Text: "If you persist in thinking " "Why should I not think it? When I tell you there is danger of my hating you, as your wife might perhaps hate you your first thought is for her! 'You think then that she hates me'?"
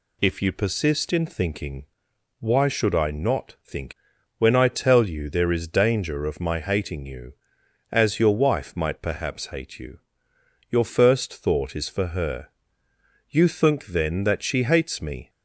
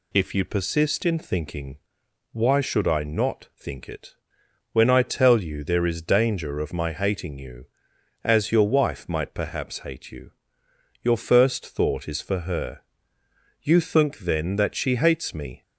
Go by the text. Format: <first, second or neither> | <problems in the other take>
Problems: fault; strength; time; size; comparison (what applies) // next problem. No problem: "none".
second | skips "it"; at 4.1 s // pauses between "you" and "your"; noticeable; at 9.9 s; 0.70 s long; noticeable in the second